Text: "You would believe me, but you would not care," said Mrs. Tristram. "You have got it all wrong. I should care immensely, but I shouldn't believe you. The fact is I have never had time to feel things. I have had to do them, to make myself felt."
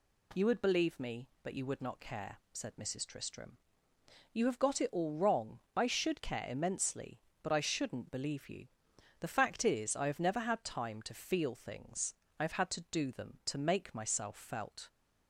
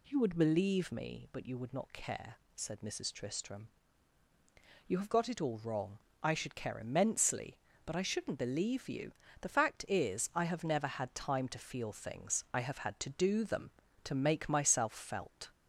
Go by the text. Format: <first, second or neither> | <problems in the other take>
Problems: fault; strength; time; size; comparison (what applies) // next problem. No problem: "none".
neither | none